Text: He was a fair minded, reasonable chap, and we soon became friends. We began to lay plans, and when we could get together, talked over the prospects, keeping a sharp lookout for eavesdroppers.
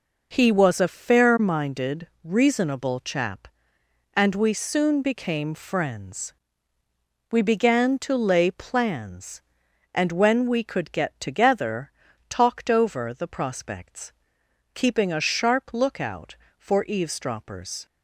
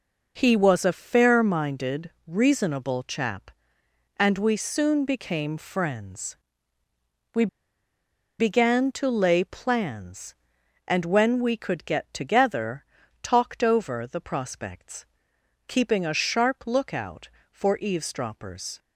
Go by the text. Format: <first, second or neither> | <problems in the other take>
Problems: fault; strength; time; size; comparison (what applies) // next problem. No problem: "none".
first | pauses between "We" and "began"; noticeable; at 7.4 s; 0.93 s long